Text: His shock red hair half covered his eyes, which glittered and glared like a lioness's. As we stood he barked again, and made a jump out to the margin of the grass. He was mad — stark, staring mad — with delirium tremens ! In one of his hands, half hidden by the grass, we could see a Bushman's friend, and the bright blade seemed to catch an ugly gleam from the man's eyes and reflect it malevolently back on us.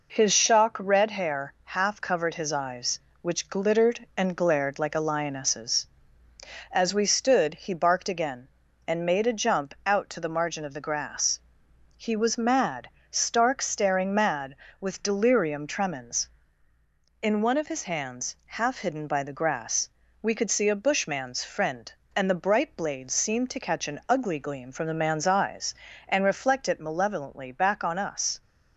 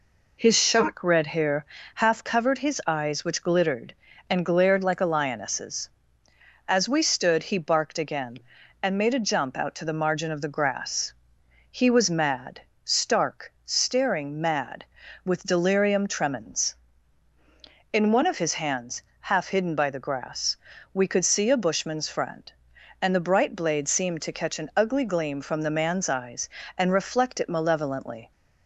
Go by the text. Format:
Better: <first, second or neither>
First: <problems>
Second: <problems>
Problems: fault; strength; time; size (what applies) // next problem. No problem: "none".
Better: first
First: none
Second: pauses between "hair" and "half"; slight; at 1.6 s; 0.30 s long // stops before "back on us"; at 28.3 s